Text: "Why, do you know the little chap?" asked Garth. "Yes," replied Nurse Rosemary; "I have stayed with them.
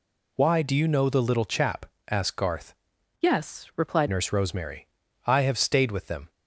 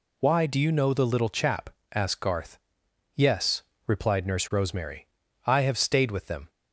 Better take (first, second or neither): second